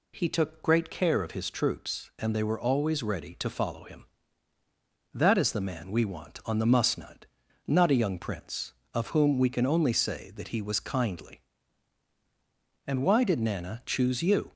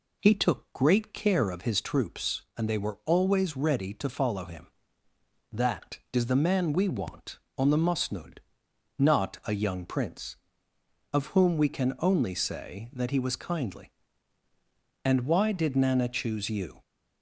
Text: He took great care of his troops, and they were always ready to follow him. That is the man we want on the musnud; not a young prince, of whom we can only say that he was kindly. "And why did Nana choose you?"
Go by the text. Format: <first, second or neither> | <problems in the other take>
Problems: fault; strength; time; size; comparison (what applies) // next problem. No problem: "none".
neither | none